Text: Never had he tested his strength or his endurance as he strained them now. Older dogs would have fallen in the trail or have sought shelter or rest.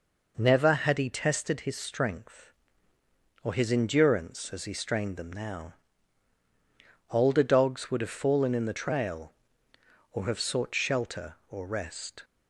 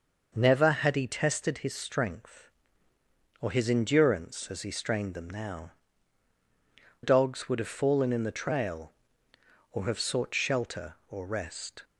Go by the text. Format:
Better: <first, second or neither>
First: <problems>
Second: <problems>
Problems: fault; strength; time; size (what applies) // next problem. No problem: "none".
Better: first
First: none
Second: starts louder than the rest; noticeable; until 1.3 s; 6 dB // skips "Older"; at 6.3 s